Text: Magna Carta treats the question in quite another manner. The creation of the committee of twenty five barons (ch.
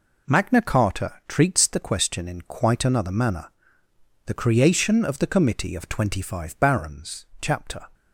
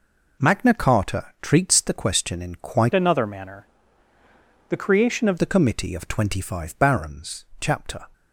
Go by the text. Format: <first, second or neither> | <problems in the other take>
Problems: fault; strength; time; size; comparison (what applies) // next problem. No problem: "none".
first | changes voice from "another" to "of"; from 2.9 to 5.3 s; 2.4 s long